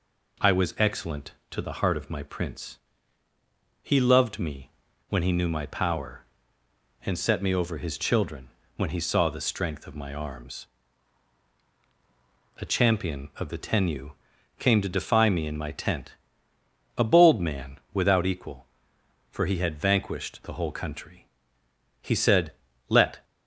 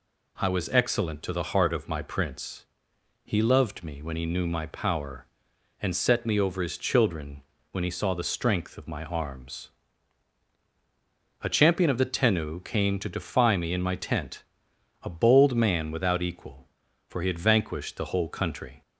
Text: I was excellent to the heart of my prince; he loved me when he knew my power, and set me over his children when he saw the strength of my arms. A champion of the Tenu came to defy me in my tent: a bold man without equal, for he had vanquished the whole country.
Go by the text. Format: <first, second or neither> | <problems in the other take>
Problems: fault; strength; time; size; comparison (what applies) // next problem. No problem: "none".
second | pauses between "me" and "when"; at 4.6 s; 0.40 s long // pauses between "children" and "when"; slight; at 8.4 s; 0.26 s long; slight in the second // pauses between "Tenu" and "came"; noticeable; at 14.1 s; 0.48 s long // goes on to say "He said Let"; noticeable; from 21.9 s on; 1.2 s long